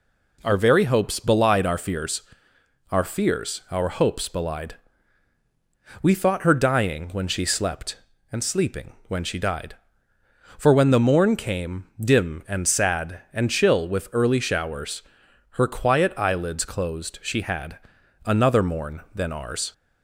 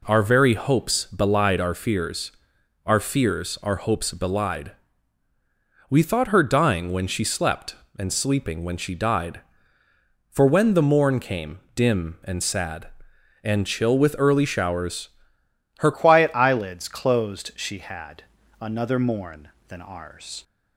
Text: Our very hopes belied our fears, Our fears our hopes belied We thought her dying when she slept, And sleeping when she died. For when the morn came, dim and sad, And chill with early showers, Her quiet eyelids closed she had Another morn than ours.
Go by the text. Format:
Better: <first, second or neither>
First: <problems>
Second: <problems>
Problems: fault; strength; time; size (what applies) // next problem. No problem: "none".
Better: first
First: pauses between "belied" and "We"; strong; at 4.7 s; 1.2 s long // pauses between "had" and "Another"; noticeable; at 17.7 s; 0.46 s long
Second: pauses between "belied" and "We"; at 4.7 s; 1.1 s long // changes voice at "quiet"; from 15.9 s on; 4.5 s long // pauses between "had" and "Another"; slight; at 18.2 s; 0.36 s long